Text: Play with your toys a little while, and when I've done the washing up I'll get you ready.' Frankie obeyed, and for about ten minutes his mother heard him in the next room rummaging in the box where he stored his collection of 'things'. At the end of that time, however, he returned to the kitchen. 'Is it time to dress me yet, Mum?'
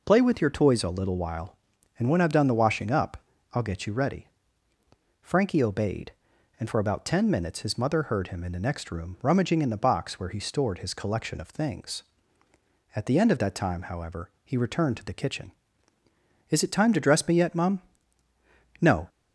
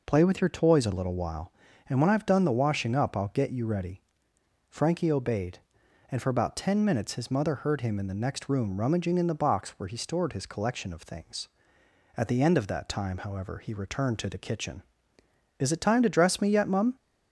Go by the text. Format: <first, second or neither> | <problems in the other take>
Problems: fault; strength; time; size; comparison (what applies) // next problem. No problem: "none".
second | pauses between "up" and "I'll"; at 3.1 s; 0.38 s long // goes on to say "No"; slight; from 18.8 s on; 0.26 s long